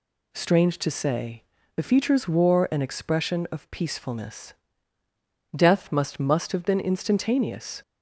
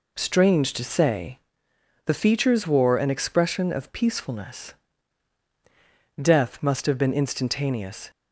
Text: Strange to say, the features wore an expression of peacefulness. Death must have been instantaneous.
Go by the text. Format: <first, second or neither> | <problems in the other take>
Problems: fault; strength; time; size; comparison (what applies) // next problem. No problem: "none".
second | says "must" twice; at 6.1 s